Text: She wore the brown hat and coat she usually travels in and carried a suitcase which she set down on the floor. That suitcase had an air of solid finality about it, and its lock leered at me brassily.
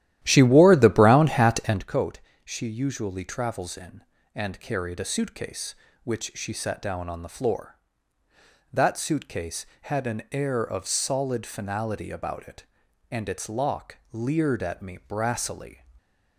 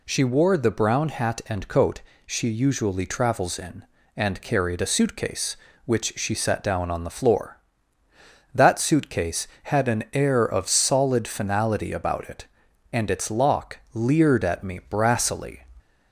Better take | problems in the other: second | starts louder than the rest; strong; until 1.8 s; 13 dB // pauses between "coat" and "she"; slight; at 2.1 s; 0.24 s long; slight in the second // pauses between "lock" and "leered"; slight; at 13.9 s; 0.16 s long; slight in the second // stays silent after the last word; slight; from 15.7 s on; 0.6 s long

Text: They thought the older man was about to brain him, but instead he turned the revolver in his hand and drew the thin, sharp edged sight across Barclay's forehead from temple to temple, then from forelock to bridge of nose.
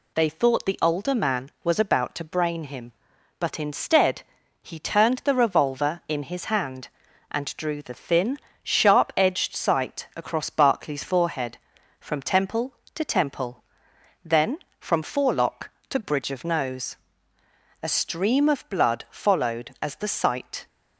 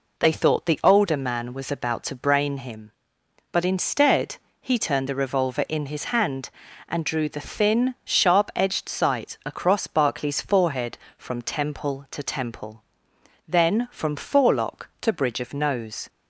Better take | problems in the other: second | pauses between "instead" and "he"; at 4.2 s; 0.38 s long; slight in the second // goes on to say "A stream of blood followed as the sight"; strong; from 17.8 s on; 2.8 s long

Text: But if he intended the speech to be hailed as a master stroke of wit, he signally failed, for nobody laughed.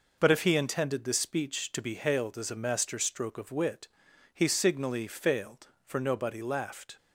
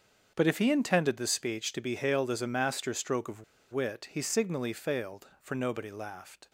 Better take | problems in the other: first | starts louder than the rest; until 1.3 s; 7 dB // pauses between "of" and "wit"; slight; at 3.4 s; 0.29 s long

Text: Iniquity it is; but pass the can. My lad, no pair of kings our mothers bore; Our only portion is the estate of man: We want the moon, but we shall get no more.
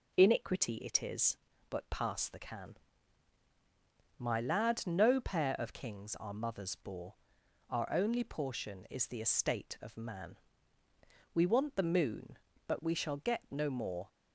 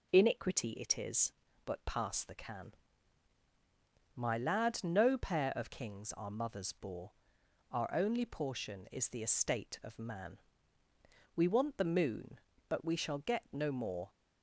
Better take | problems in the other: neither | none

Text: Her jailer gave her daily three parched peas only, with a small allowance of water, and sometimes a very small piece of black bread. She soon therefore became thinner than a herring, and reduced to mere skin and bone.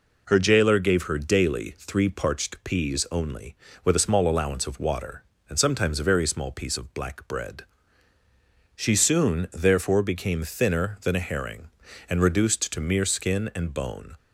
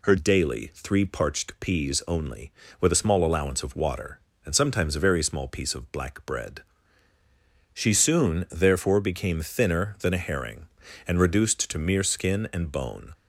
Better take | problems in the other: first | skips "jailer gave her"; at 0.1 s

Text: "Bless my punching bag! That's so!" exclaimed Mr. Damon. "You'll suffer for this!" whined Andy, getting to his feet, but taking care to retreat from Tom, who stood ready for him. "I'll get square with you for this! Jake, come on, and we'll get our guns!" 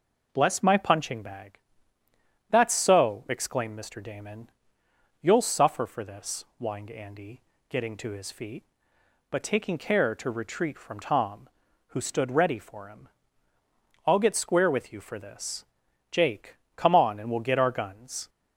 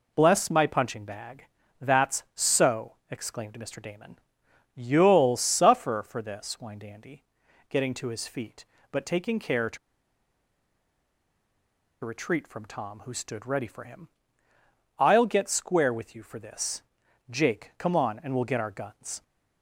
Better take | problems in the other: first | pauses between "to" and "retreat"; strong; at 9.7 s; 2.2 s long

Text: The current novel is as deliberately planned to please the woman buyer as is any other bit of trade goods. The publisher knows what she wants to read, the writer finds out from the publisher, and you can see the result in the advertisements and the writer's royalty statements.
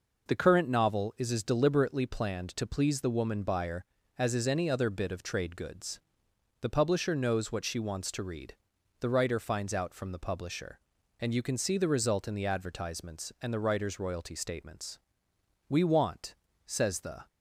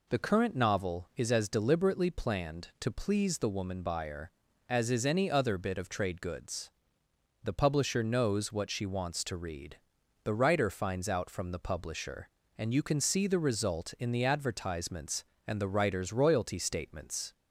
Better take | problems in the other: second | goes on to say "We want says the"; from 15.6 s on; 1.5 s long

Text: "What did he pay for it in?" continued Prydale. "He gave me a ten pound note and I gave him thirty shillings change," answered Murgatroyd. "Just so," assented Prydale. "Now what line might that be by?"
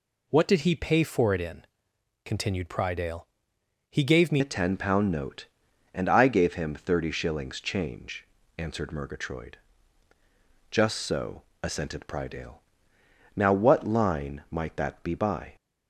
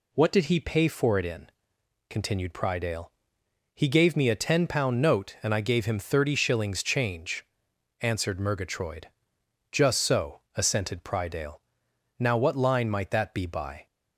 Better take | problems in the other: second | changes voice at "a"; from 4.4 s on; 11.1 s long

